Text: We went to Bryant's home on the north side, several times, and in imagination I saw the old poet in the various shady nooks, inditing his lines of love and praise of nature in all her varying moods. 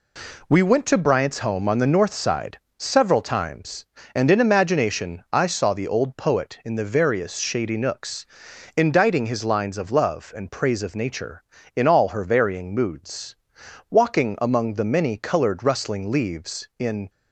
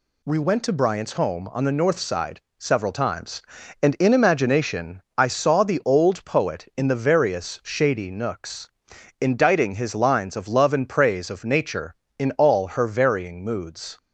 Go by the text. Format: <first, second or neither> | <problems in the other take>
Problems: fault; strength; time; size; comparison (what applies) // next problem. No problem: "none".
second | goes on to say "Walking among the many colored rustling leaves in"; strong; from 13.8 s on; 3.2 s long